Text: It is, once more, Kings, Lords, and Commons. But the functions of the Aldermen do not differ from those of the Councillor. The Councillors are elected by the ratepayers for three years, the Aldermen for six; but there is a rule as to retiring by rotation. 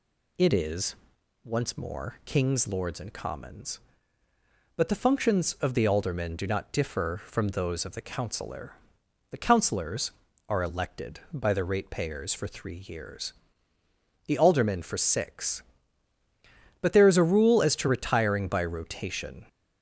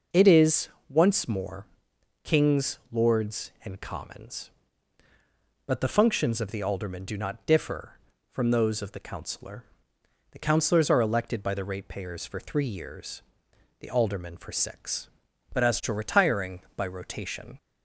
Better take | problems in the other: first | skips "there is a rule"; at 15.6 s

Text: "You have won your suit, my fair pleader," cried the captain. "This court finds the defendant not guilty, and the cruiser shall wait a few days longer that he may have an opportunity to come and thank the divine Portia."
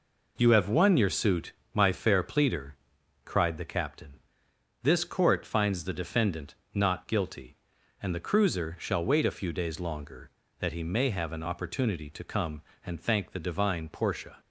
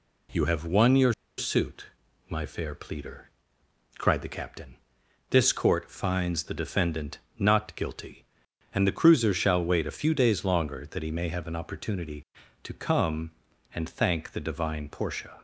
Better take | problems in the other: first | pauses between "your" and "suit"; slight; at 1.1 s; 0.25 s long // pauses between "defendant" and "not"; slight; at 7.1 s; 0.18 s long; slight in the first

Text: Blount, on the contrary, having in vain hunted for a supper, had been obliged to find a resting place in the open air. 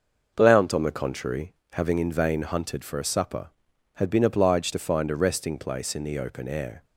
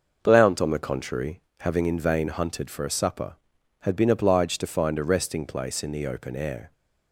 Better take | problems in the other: neither | none

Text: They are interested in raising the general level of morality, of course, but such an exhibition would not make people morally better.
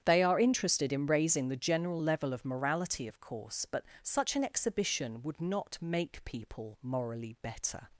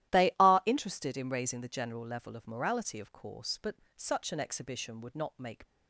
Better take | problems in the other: first | starts louder than the rest; strong; until 1.2 s; 13.5 dB; strong in the first // pauses between "but" and "such"; slight; at 3.7 s; 0.22 s long; slight in the first // stops before "people morally better"; at 5.6 s

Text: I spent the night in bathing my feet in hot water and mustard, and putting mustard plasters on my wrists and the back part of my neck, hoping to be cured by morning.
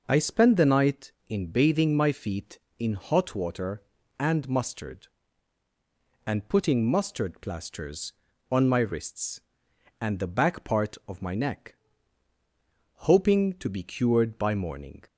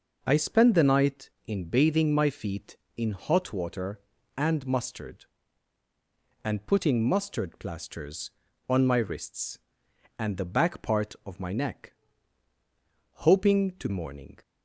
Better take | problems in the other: first | skips "be cured by"; at 13.9 s

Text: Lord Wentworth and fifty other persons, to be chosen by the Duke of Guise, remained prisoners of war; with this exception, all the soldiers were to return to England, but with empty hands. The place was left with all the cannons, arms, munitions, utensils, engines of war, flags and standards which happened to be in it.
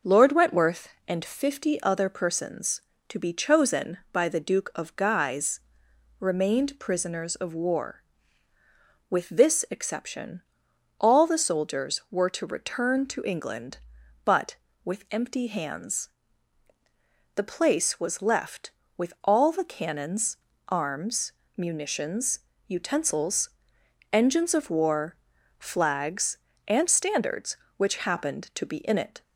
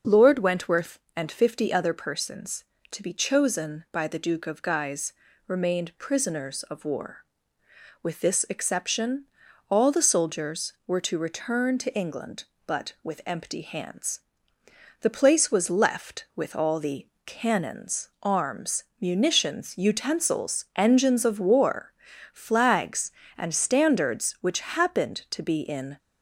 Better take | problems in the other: first | pauses between "the" and "cannons"; slight; at 17.0 s; 0.18 s long // stops before "it"; at 25.9 s

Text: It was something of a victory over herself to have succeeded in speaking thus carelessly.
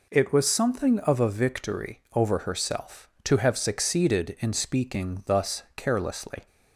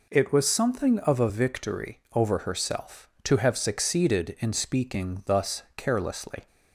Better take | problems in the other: neither | none

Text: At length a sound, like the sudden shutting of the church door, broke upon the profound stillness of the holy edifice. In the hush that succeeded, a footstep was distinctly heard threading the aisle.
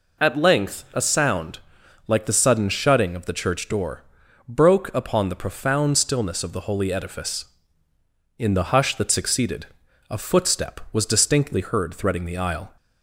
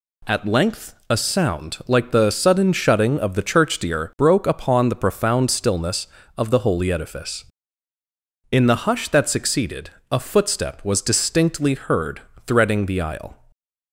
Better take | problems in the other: first | says "deer" for "door"; at 3.7 s // pauses between "heard" and "threading"; slight; at 12.2 s; 0.24 s long

